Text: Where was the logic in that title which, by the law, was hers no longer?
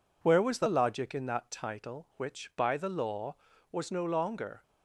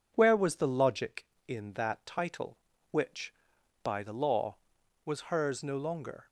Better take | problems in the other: second | skips "hers"; at 3.9 s

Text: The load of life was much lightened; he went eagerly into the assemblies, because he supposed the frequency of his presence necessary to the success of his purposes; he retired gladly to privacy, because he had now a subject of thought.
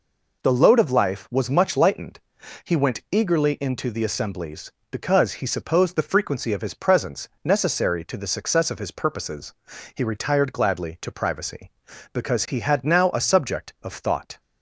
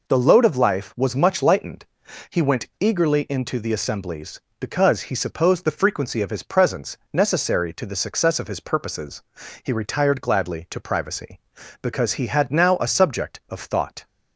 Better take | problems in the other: neither | pauses between "presence" and "necessary"; slight; the same in both

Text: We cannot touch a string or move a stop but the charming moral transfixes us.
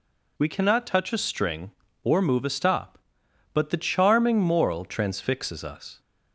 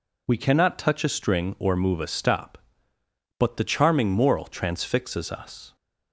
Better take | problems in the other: neither | none

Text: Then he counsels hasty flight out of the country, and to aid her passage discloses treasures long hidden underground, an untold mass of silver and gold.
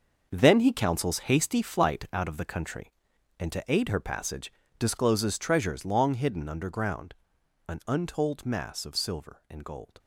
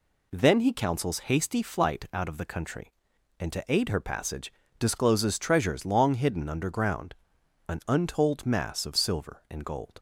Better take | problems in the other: second | gets quieter; strong; throughout; 10.5 dB // pauses between "passage" and "discloses"; slight; at 4.5 s; 0.26 s long; slight in the second

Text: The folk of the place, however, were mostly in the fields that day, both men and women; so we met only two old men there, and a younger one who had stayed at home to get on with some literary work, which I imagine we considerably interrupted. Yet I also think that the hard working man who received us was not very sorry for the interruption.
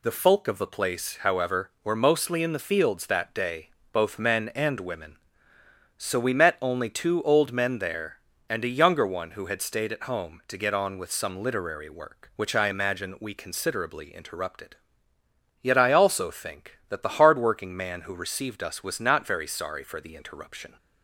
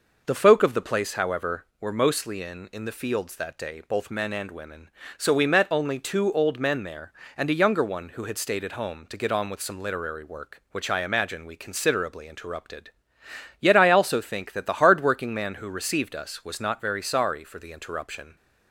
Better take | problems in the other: first | says "in" twice; at 2.7 s

